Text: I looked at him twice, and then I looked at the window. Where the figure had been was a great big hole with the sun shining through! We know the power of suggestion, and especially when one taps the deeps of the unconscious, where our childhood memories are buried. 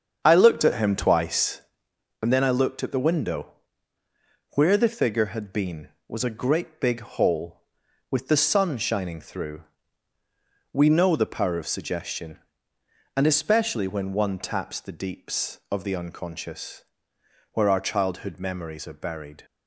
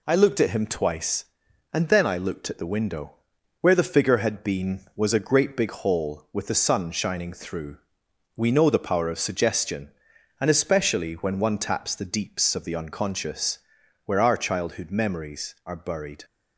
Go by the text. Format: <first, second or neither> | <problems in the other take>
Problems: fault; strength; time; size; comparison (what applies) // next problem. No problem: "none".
second | starts louder than the rest; strong; until 1.9 s; 7.5 dB